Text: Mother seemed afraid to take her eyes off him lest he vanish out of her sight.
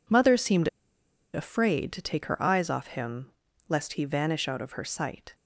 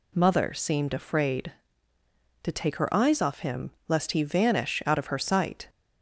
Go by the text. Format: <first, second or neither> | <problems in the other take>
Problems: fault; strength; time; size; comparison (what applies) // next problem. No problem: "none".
second | pauses between "seemed" and "afraid"; noticeable; at 0.6 s; 0.66 s long // pauses between "him" and "lest"; at 3.3 s; 0.38 s long; slight in the second